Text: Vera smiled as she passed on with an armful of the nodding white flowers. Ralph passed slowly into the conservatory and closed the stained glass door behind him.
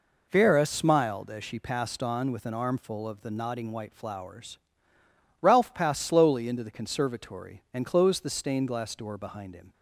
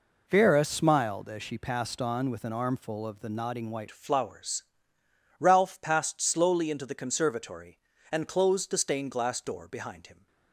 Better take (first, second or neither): first